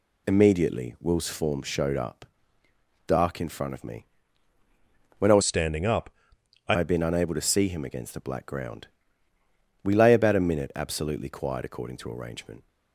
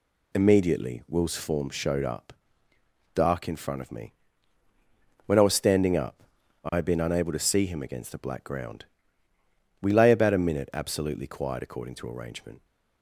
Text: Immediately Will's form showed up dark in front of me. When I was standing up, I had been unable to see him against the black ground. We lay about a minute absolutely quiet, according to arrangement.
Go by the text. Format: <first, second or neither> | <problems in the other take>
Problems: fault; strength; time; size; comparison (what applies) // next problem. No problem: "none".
second | pauses between "up" and "dark"; noticeable; at 2.2 s; 0.82 s long; noticeable in the second // changes voice from "standing" to "I"; from 5.4 to 6.7 s; 1.3 s long